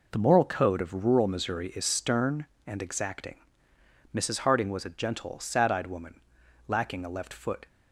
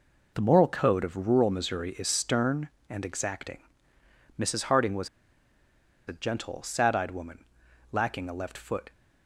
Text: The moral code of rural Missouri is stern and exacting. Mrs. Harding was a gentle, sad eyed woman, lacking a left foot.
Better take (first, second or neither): first